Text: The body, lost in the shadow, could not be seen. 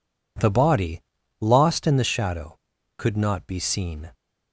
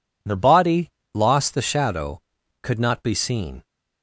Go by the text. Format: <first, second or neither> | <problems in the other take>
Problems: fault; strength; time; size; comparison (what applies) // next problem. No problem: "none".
first | skips "in"; at 1.5 s